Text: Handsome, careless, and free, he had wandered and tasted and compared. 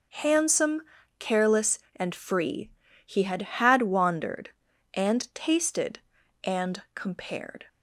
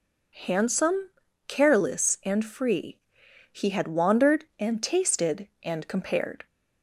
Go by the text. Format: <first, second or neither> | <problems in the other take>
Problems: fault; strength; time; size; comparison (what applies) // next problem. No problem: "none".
second | says "had" twice; at 3.4 s